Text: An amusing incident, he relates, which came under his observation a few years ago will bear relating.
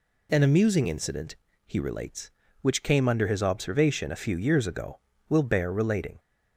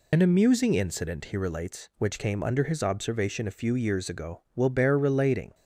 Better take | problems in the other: first | loses the start of "An"; at 0.1 s; 45 ms

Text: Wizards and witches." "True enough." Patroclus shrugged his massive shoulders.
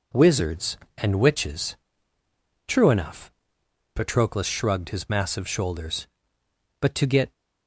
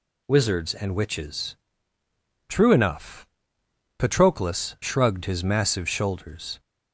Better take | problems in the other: second | goes on to say "But to get"; from 6.8 s on; 0.50 s long

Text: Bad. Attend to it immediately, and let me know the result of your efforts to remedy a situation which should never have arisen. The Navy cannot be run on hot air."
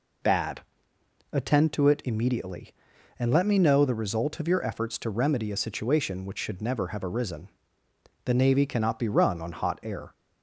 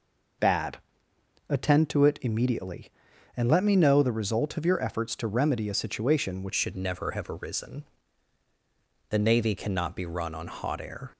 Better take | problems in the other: first | changes voice at "should"; from 6.5 s on; 4.6 s long

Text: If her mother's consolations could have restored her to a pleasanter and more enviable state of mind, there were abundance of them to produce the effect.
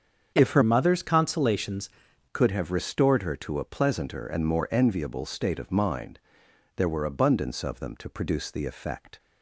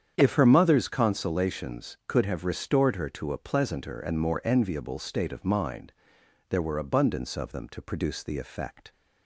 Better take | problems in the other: second | starts louder than the rest; strong; until 1.3 s; 7.5 dB; strong in the second // changes voice from "mother's" to "consolations"; from 0.6 to 1.8 s; 1.2 s long

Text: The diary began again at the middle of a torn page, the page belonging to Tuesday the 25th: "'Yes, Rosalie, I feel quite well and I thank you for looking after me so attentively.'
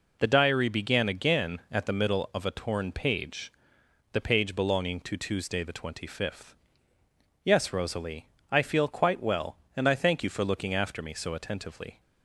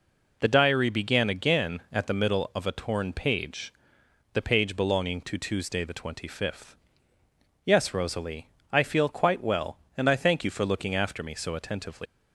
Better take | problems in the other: first | leaves "attentively" unfinished; at 12.0 s; 150 ms

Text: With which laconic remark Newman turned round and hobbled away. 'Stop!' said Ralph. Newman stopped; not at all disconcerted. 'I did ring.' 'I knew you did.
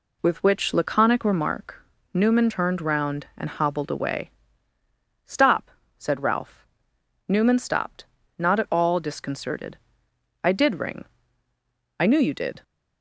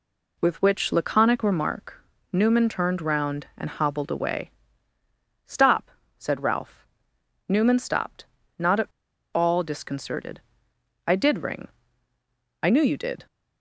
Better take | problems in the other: first | pauses between "remark" and "Newman"; slight; at 2.0 s; 0.28 s long; slight in the first // pauses between "at" and "all"; noticeable; at 8.8 s; 0.48 s long

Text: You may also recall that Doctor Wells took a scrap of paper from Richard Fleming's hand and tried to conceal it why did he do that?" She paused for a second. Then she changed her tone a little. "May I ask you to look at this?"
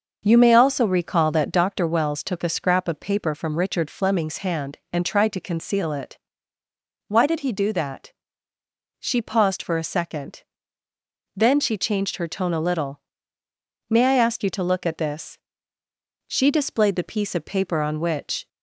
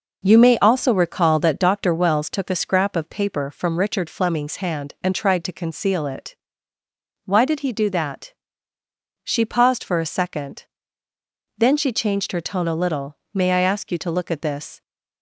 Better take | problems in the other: second | starts louder than the rest; until 1.2 s; 6 dB // pauses between "it" and "why"; noticeable; at 6.1 s; 0.90 s long; noticeable in the second // goes on to say "She displayed the piece of paper on which"; strong; from 16.2 s on; 2.2 s long

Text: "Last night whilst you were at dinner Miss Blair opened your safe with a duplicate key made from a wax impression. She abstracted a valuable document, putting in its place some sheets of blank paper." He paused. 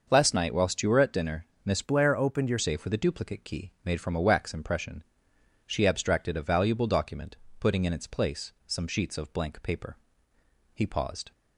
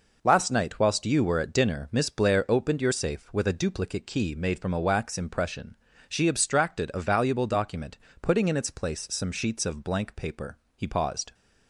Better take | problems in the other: second | starts louder than the rest; noticeable; until 1.1 s; 6 dB // pauses between "dinner" and "Miss"; slight; at 1.4 s; 0.22 s long // changes voice from "Blair" to "your"; from 1.8 to 2.5 s; 0.7 s long // pauses between "place" and "some"; slight; at 8.5 s; 0.16 s long

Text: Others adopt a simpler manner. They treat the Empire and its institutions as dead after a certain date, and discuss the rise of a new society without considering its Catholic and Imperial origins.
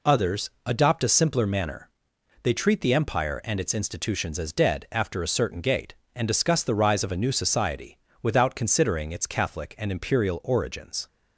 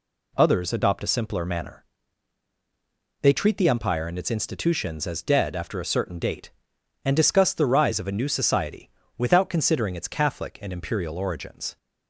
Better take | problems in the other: second | pauses between "Others" and "adopt"; slight; at 0.4 s; 0.16 s long // says "gate" for "date"; at 5.6 s // pauses between "society" and "without"; slight; at 7.9 s; 0.24 s long; slight in the second

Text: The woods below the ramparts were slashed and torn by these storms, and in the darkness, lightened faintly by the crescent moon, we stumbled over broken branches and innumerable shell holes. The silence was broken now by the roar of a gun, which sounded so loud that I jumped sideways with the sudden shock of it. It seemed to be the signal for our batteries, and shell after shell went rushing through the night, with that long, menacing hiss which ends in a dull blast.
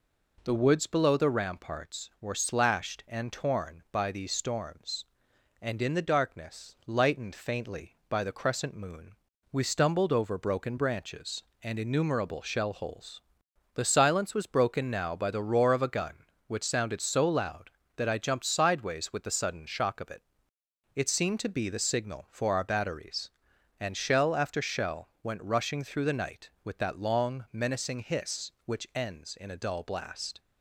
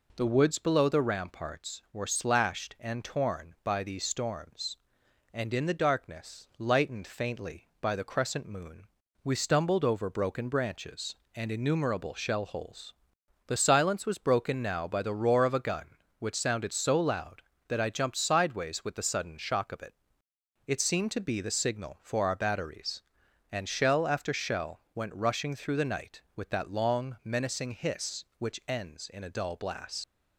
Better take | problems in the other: first | pauses between "shell" and "went"; slight; at 24.7 s; 0.16 s long; slight in the first // leaves "blast" unfinished; at 30.0 s; 85 ms

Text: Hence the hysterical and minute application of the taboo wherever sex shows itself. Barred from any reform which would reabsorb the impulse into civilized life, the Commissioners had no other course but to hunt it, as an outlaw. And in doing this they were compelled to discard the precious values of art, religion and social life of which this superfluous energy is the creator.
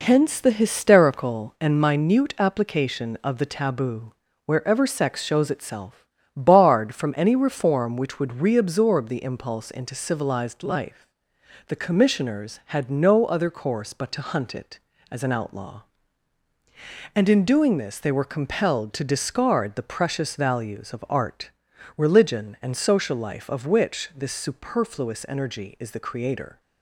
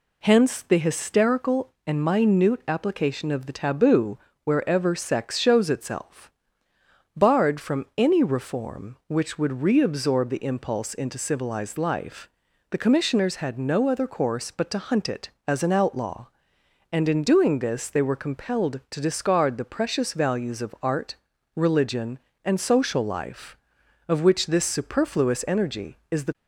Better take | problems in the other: first | pauses between "taboo" and "wherever"; slight; at 4.1 s; 0.26 s long; slight in the first // stops before "creator"; at 26.3 s

